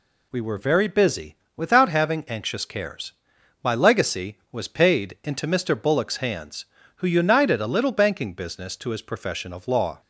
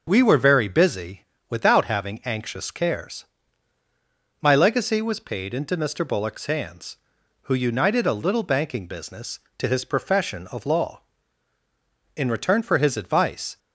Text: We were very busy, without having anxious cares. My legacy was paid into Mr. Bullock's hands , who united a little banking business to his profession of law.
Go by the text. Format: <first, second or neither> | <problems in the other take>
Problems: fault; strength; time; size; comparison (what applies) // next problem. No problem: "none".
first | goes on to say "In return for his advice"; from 12.1 s on; 1.4 s long